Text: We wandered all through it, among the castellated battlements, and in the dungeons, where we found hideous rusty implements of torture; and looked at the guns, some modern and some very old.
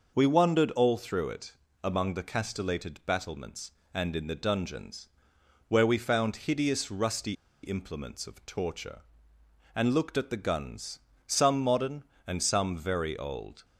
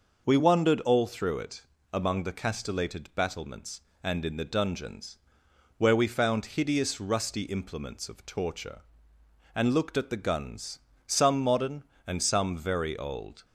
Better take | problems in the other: second | pauses between "rusty" and "implements"; slight; at 7.3 s; 0.29 s long

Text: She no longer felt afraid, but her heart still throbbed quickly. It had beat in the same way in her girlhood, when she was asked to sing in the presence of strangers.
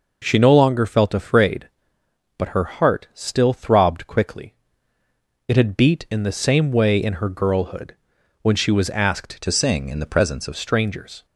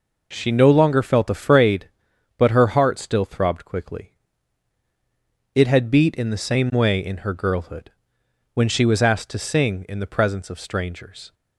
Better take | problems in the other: second | changes voice from "to" to "of"; from 9.4 to 10.5 s; 1.1 s long

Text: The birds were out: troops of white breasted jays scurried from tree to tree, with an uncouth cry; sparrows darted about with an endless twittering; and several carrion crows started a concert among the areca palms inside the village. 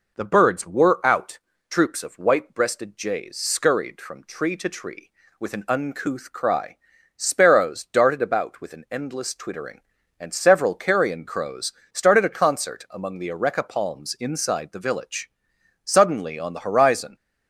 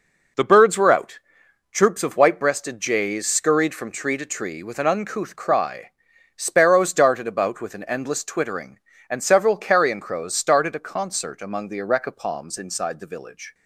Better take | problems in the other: second | pauses between "crows" and "started"; slight; at 11.7 s; 0.22 s long // goes on to say "Suddenly on the horizon"; noticeable; from 15.8 s on; 1.3 s long

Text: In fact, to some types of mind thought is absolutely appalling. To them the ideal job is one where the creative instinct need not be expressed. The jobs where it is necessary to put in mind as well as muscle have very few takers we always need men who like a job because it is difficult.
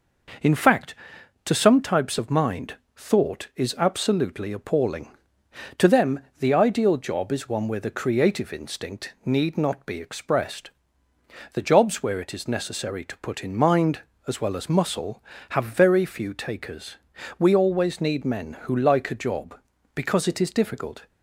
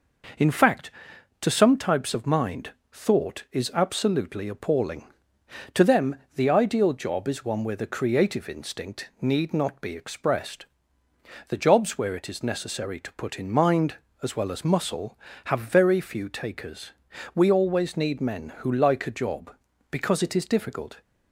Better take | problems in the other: neither | pauses between "mind" and "thought"; slight; the same in both // pauses between "them" and "the"; slight; the same in both // pauses between "takers" and "we"; the same in both

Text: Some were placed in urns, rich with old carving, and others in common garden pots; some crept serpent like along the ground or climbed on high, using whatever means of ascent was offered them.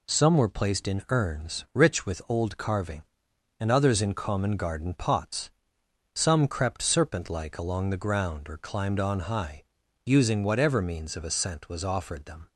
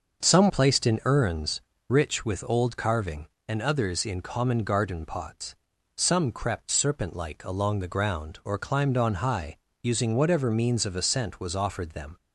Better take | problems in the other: first | starts louder than the rest; until 1.3 s; 6.5 dB // skips "were"; at 0.4 s

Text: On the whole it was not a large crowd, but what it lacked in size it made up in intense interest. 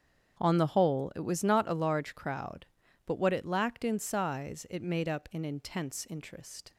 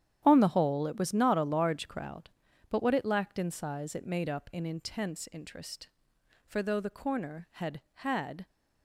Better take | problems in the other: first | starts louder than the rest; strong; until 1.2 s; 10 dB; strong in the first // goes on to say "For though The Corner had had"; strong; from 6.4 s on; 2.0 s long

